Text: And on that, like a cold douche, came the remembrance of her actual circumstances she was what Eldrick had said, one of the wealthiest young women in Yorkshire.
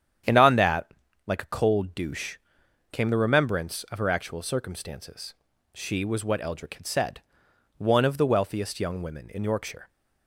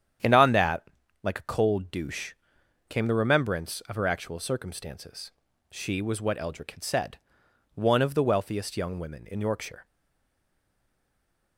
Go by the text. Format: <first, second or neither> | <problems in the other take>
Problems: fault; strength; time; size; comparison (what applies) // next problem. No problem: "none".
first | starts louder than the rest; strong; until 1.5 s; 9 dB; strong in the first // pauses between "circumstances" and "she"; at 5.3 s; 0.40 s long; also in the first // stays silent after the last word; noticeable; from 9.8 s on; 1.7 s long